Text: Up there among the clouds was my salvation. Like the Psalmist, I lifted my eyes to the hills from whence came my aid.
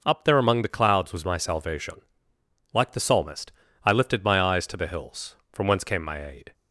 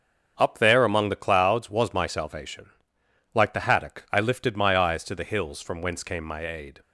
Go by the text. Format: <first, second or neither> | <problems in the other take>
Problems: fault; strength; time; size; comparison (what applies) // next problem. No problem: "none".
first | starts louder than the rest; until 1.3 s; 6.5 dB // says "Haddock" for "Psalmist"; at 3.6 s